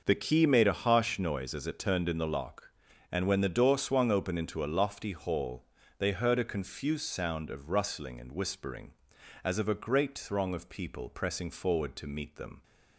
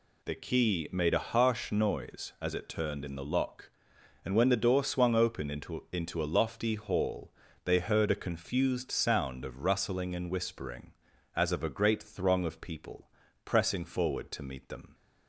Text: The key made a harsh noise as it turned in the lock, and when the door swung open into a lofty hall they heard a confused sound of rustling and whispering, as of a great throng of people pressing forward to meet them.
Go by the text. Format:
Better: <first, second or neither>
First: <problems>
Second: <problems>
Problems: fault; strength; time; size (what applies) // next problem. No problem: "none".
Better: first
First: pauses between "hall" and "they"; slight; at 5.6 s; 0.36 s long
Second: says "into" twice; at 5.9 s // pauses between "hall" and "they"; slight; at 7.3 s; 0.32 s long // pauses between "people" and "pressing"; slight; at 13.1 s; 0.34 s long